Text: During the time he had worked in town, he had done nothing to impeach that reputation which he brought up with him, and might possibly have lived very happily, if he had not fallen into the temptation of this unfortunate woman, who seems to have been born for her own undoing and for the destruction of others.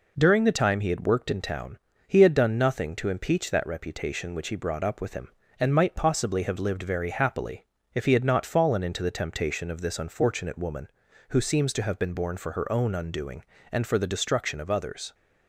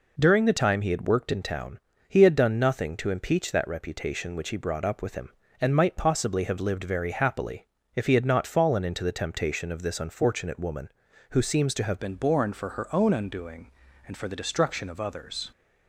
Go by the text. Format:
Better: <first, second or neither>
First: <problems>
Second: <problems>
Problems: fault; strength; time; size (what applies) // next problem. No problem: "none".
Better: first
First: none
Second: changes voice at "been"; from 11.9 s on; 3.5 s long